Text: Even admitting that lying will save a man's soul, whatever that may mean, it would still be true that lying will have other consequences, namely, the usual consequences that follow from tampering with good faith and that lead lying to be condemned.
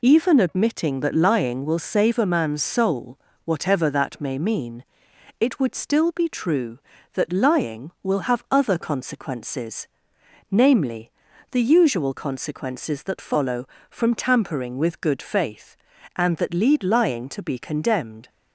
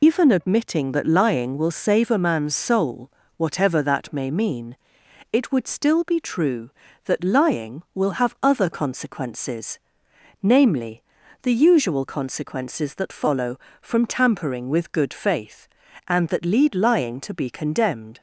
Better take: first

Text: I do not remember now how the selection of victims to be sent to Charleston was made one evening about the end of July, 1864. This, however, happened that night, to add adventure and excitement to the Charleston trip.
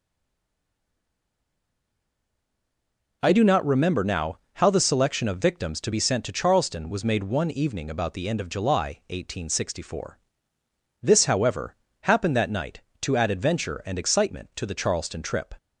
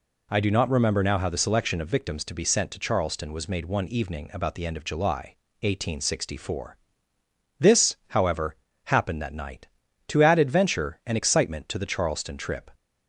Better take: second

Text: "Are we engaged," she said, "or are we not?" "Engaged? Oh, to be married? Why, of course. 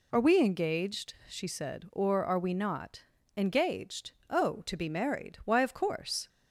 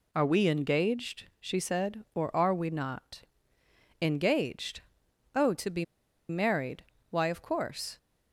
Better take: first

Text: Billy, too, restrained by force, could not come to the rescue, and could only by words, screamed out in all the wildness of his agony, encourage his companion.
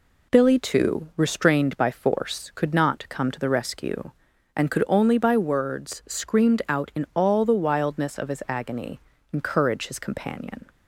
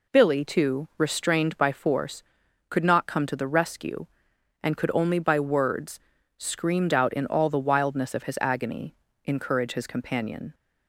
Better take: neither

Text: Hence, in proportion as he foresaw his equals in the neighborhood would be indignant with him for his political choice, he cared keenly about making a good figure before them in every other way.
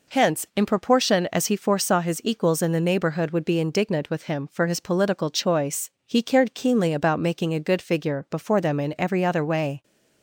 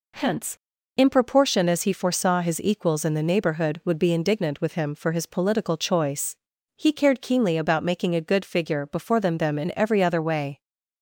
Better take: first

